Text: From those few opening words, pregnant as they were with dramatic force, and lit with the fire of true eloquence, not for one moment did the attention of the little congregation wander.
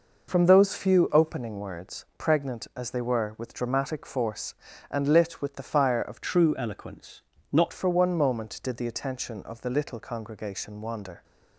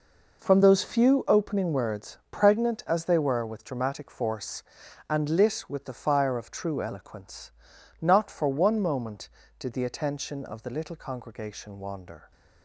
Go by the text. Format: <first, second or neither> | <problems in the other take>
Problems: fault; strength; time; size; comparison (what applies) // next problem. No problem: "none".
second | changes voice from "true" to "not"; from 6.2 to 7.7 s; 1.5 s long